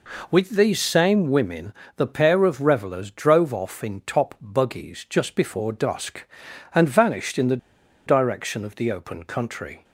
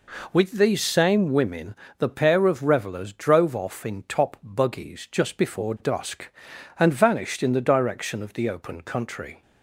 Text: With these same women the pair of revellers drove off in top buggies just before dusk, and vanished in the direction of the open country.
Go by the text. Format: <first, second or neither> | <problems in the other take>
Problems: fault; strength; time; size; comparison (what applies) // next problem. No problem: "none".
second | pauses between "women" and "the"; slight; at 1.7 s; 0.24 s long; slight in the second // pauses between "the" and "direction"; noticeable; at 7.5 s; 0.49 s long